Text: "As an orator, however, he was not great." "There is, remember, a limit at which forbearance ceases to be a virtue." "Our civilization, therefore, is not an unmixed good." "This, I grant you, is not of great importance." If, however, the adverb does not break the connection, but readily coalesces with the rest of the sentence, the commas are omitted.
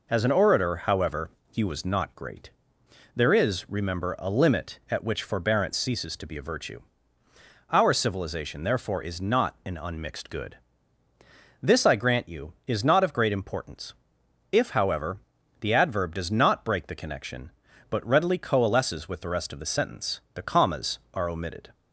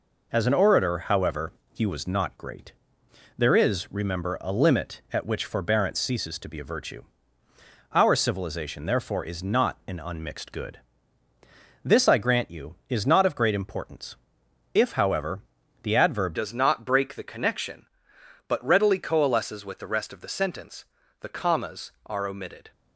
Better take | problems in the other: first | changes voice at "does"; from 16.3 s on; 6.4 s long

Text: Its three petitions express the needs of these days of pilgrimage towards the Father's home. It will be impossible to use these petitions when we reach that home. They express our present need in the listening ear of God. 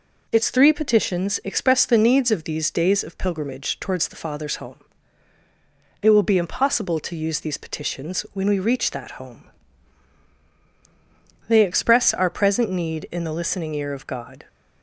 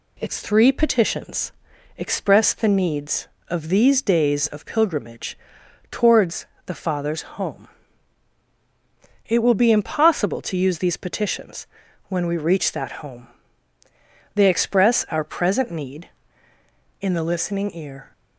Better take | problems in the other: first | pauses between "petitions" and "express"; at 1.5 s; 0.44 s long // pauses between "pilgrimage" and "towards"; noticeable; at 5.3 s; 0.54 s long // pauses between "towards" and "the"; slight; at 6.4 s; 0.20 s long // pauses between "petitions" and "when"; at 11.6 s; 0.42 s long // stops before "of God"; at 18.1 s

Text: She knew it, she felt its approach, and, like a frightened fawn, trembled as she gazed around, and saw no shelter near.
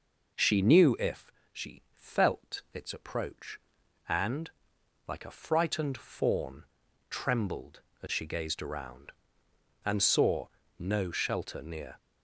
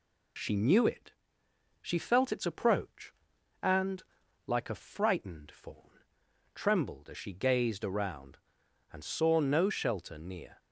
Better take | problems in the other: second | says "if" for "it"; at 0.9 s // pauses between "saw" and "no"; slight; at 10.4 s; 0.30 s long

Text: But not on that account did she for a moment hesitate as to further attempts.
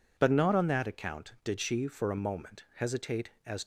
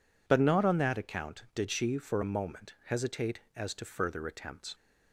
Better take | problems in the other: second | stops before "to further attempts"; at 3.6 s

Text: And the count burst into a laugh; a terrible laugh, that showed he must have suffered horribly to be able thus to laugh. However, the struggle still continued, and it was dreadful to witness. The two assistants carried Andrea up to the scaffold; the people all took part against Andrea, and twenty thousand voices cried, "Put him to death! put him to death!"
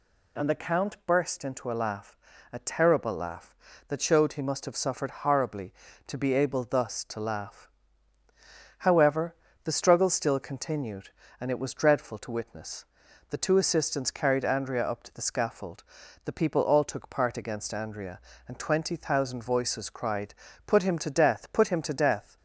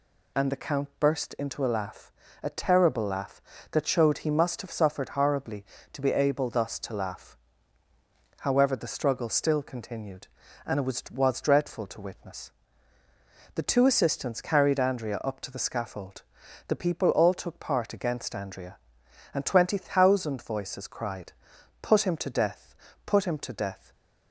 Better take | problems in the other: first | says "was" twice; at 11.1 s // stays silent after the last word; slight; from 23.7 s on; 0.6 s long

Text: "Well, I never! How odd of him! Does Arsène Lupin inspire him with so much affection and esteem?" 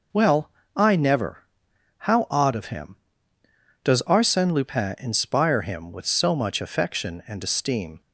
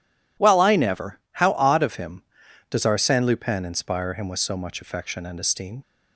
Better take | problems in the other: neither | none

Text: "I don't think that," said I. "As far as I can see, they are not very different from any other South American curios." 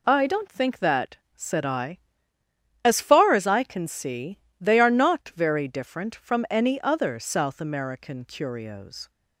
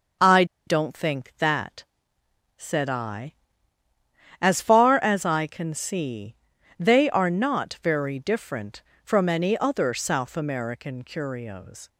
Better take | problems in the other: first | starts louder than the rest; until 1.4 s; 6.5 dB // pauses between "I" and "don't"; slight; at 0.4 s; 0.22 s long

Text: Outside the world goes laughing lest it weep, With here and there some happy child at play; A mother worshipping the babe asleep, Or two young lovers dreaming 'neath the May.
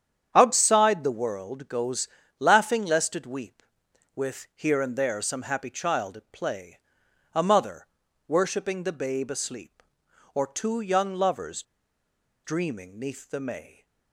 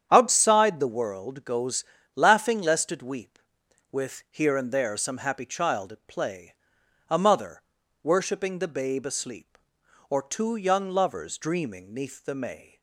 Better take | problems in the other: second | starts louder than the rest; strong; until 1.3 s; 8.5 dB; strong in the second // pauses between "goes" and "laughing"; slight; at 2.0 s; 0.32 s long; slight in the second // pauses between "mother" and "worshipping"; at 7.8 s; 0.40 s long; also in the second // pauses between "lovers" and "dreaming"; noticeable; at 11.6 s; 0.82 s long

